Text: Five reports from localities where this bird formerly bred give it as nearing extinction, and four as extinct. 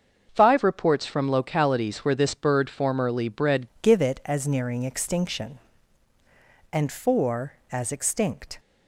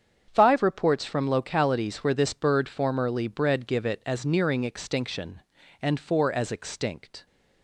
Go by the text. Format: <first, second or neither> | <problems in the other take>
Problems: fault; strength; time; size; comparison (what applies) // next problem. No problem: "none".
second | starts louder than the rest; until 1.3 s; 6.5 dB; strong in the second // changes voice at "give"; from 3.8 s on; 4.7 s long